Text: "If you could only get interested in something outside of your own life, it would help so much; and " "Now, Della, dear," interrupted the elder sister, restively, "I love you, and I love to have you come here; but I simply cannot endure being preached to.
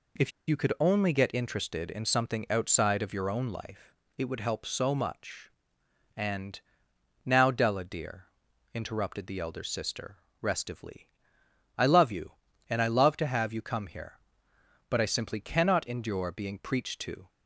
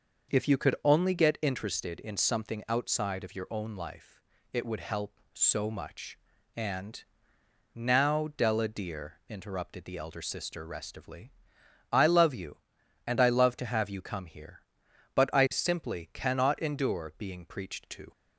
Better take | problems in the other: second | pauses between "If" and "you"; slight; at 0.3 s; 0.18 s long

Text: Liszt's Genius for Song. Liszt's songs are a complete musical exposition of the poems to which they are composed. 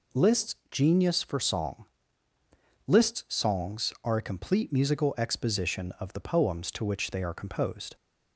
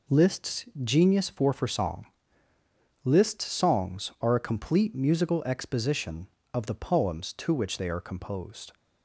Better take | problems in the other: first | pauses between "Liszt's" and "Genius"; slight; at 0.6 s; 0.18 s long // says "for" twice; at 1.5 s

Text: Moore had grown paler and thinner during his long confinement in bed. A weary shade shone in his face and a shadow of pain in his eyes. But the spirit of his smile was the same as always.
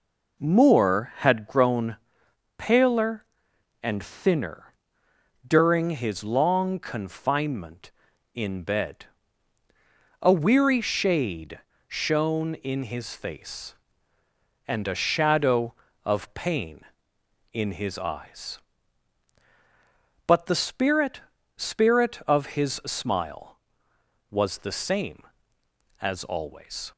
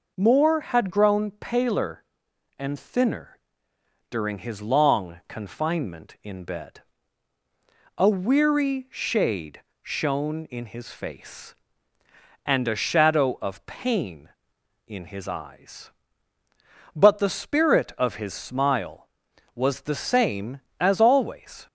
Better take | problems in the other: second | pauses between "grown" and "paler"; noticeable; at 1.9 s; 0.62 s long // pauses between "thinner" and "during"; noticeable; at 4.7 s; 0.74 s long; noticeable in the second // pauses between "shade" and "shone"; slight; at 11.5 s; 0.28 s long; slight in the second // says "spirit" twice; at 21.5 s

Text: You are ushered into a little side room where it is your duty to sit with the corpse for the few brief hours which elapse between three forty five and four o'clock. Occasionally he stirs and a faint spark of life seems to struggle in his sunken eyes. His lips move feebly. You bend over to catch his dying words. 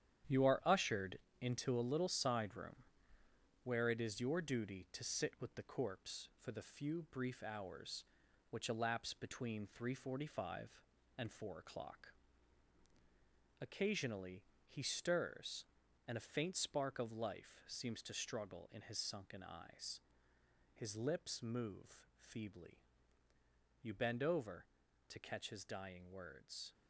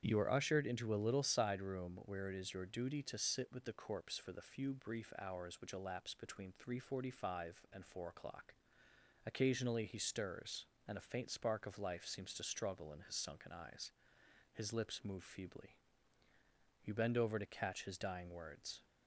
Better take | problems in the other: second | gets quieter; strong; throughout; 8.5 dB // starts louder than the rest; strong; until 1.5 s; 10 dB; strong in the second // pauses between "ushered" and "into"; slight; at 1.1 s; 0.20 s long // pauses between "room" and "where"; noticeable; at 2.7 s; 0.84 s long // pauses between "Occasionally" and "he"; slight; at 14.4 s; 0.24 s long

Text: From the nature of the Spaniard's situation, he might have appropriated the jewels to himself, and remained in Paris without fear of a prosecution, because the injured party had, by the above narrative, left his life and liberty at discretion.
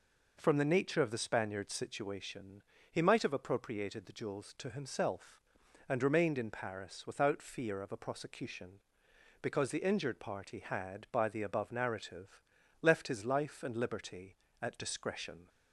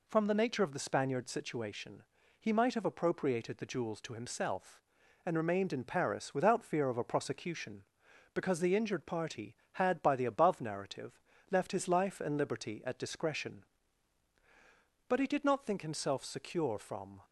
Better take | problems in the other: first | goes on to say "But he did not think himself secure from"; strong; from 15.0 s on; 2.1 s long

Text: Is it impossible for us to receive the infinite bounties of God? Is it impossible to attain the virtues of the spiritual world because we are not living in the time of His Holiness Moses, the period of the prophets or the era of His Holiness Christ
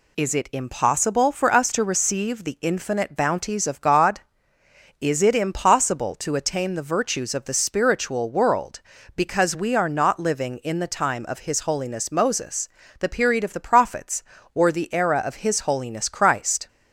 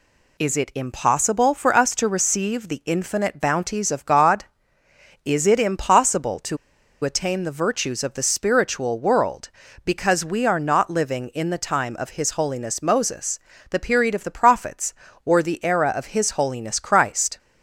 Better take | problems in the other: first | pauses between "to" and "attain"; noticeable; at 6.5 s; 0.47 s long

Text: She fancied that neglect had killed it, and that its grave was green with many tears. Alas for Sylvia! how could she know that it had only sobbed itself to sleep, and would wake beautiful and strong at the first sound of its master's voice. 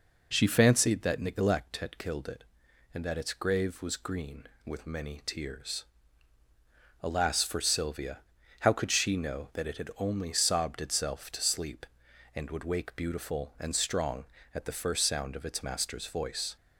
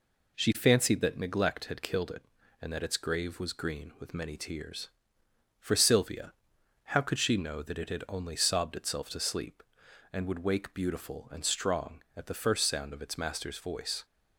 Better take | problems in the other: first | skips "Alas"; at 5.2 s

